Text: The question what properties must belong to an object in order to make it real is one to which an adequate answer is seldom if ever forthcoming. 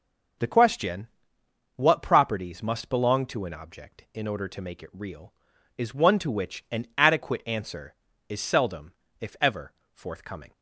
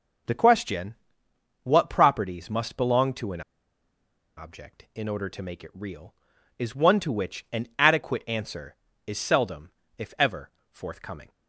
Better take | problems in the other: first | pauses between "question" and "what"; noticeable; at 0.9 s; 0.66 s long; noticeable in the first // pauses between "an" and "object"; noticeable; at 3.4 s; 0.95 s long // pauses between "seldom" and "if"; slight; at 9.7 s; 0.26 s long; slight in the first // pauses between "ever" and "forthcoming"; slight; at 10.4 s; 0.22 s long; slight in the first

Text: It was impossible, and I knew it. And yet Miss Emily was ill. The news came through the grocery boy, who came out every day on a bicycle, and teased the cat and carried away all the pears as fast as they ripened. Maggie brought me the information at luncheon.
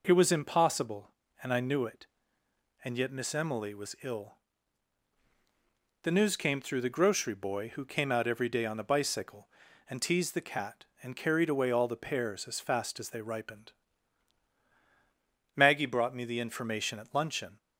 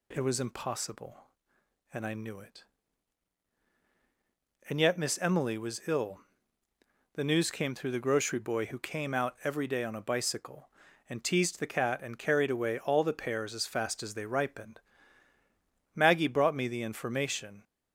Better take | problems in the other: first | stops before "at luncheon"; at 17.6 s

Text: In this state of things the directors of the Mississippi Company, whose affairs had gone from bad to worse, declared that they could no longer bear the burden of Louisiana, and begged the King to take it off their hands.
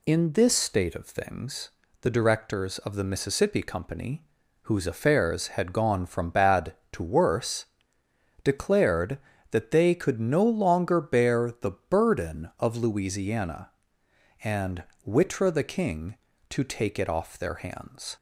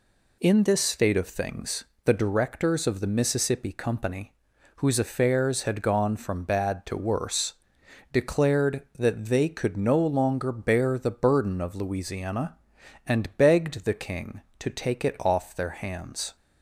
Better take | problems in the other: second | pauses between "things" and "the"; slight; at 1.7 s; 0.30 s long; slight in the second // pauses between "the" and "burden"; slight; at 11.7 s; 0.18 s long // says "witra" for "begged"; at 15.0 s

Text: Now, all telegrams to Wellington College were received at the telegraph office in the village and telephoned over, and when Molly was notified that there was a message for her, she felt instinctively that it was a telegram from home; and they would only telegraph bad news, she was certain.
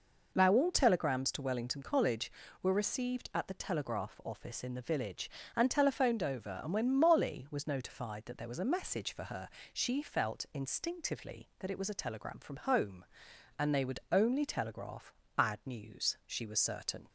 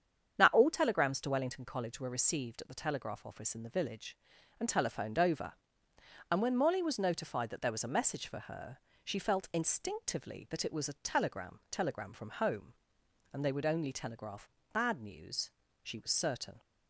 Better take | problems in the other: first | starts louder than the rest; strong; until 1.4 s; 8 dB // says "telegram" twice; at 11.6 s // pauses between "telegraph" and "bad"; slight; at 14.4 s; 0.24 s long; slight in the first

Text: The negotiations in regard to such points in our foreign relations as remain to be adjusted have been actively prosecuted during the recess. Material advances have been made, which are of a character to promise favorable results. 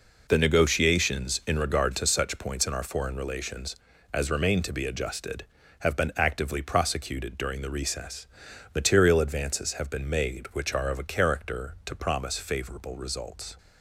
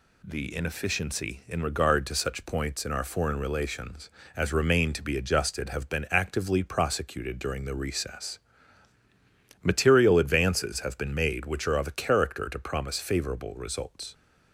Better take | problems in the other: first | says "inefficiency" for "negotiations"; at 0.5 s

